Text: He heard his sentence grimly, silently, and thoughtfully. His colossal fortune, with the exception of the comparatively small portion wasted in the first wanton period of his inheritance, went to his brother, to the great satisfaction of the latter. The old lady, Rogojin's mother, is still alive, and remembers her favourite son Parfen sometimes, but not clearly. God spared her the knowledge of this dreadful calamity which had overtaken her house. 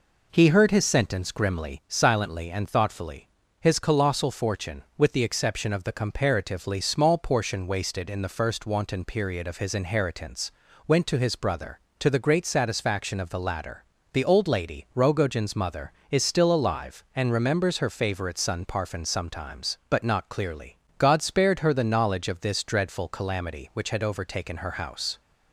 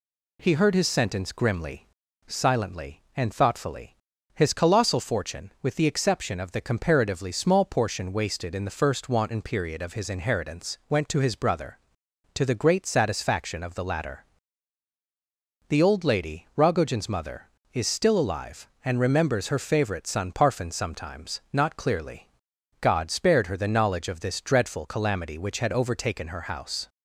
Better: first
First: none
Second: skips "but"; at 21.4 s

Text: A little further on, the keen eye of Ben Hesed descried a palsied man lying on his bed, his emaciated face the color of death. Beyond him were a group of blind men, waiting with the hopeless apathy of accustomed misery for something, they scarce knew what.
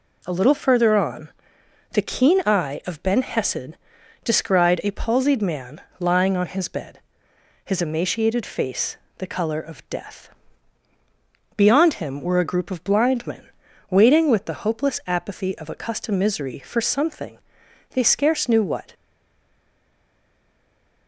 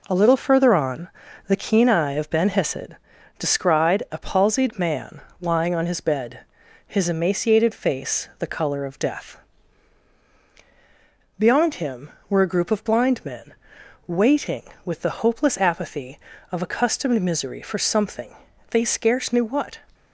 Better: second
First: pauses between "Hesed" and "descried"; noticeable; at 3.7 s; 0.48 s long // pauses between "man" and "lying"; slight; at 5.8 s; 0.18 s long // pauses between "face" and "the"; slight; at 8.9 s; 0.20 s long // stays silent after the last word; from 18.9 s on; 2.1 s long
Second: pauses between "Hesed" and "descried"; at 2.9 s; 0.42 s long // pauses between "man" and "lying"; slight; at 5.2 s; 0.18 s long

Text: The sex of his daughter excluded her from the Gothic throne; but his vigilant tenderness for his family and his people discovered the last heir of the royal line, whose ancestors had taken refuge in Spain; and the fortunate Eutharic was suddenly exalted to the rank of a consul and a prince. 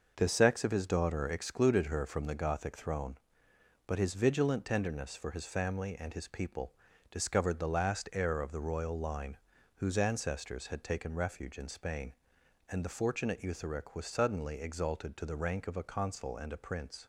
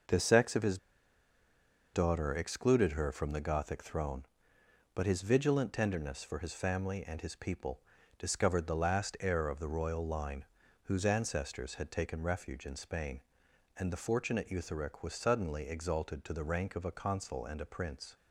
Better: first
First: pauses between "people" and "discovered"; at 6.7 s; 0.38 s long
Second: pauses between "his" and "daughter"; at 0.7 s; 1.1 s long // pauses between "people" and "discovered"; at 7.8 s; 0.38 s long

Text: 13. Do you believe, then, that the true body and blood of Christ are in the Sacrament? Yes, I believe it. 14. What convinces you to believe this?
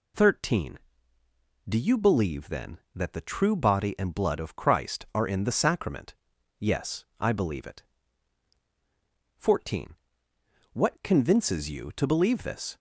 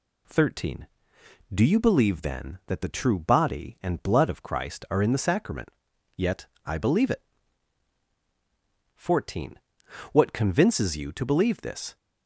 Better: first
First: none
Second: says "Yet" for "Yes"; at 6.1 s

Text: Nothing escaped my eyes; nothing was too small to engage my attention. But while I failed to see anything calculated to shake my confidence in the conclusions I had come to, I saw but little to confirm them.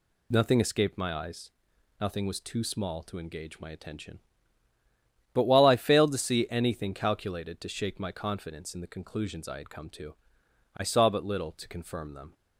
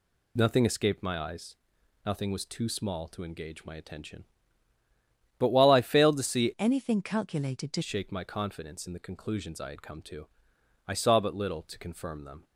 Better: first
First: none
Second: changes voice from "anything" to "to"; from 6.5 to 7.8 s; 1.3 s long

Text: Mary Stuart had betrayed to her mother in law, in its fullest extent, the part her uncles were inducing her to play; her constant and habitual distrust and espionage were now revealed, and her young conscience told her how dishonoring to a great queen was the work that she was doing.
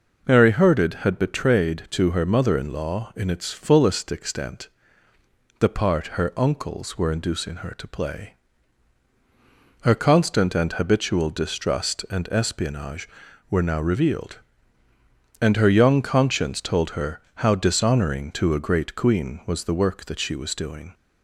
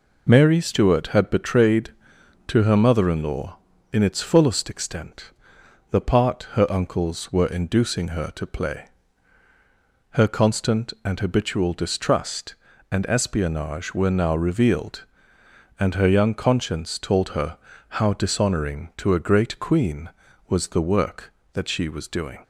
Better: second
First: says "Herded" for "Stuart"; at 0.5 s // pauses between "her" and "how"; slight; at 17.1 s; 0.24 s long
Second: pauses between "her" and "how"; slight; at 17.5 s; 0.32 s long

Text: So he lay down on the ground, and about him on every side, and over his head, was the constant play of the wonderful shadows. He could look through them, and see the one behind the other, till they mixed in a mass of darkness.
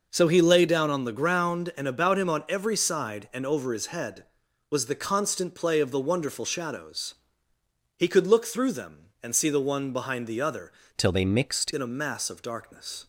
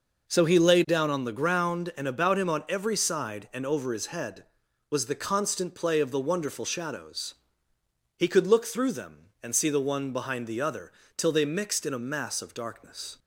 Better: second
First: changes voice from "till" to "mixed"; from 10.9 to 11.7 s; 0.8 s long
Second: none

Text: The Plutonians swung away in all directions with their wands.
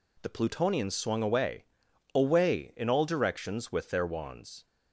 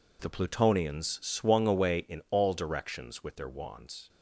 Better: second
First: says "away" twice; at 2.1 s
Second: none

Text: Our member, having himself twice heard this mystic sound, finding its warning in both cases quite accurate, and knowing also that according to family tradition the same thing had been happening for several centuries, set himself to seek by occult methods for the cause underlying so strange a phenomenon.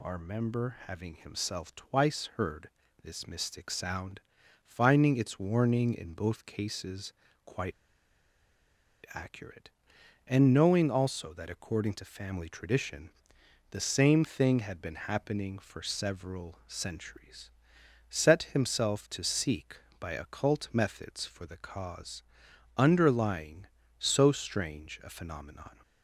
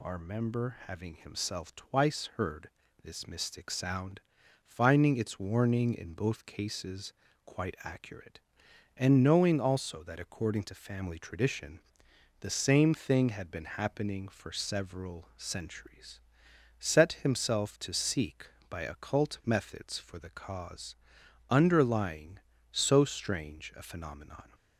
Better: second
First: pauses between "heard" and "this"; slight; at 2.6 s; 0.34 s long // pauses between "cases" and "quite"; slight; at 7.1 s; 0.32 s long // pauses between "quite" and "accurate"; strong; at 7.7 s; 1.4 s long // pauses between "tradition" and "the"; noticeable; at 13.0 s; 0.60 s long // pauses between "cause" and "underlying"; noticeable; at 22.2 s; 0.54 s long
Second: pauses between "heard" and "this"; slight; at 2.6 s; 0.34 s long // pauses between "cases" and "quite"; slight; at 7.1 s; 0.32 s long // pauses between "tradition" and "the"; noticeable; at 11.7 s; 0.60 s long // pauses between "cause" and "underlying"; noticeable; at 20.9 s; 0.54 s long

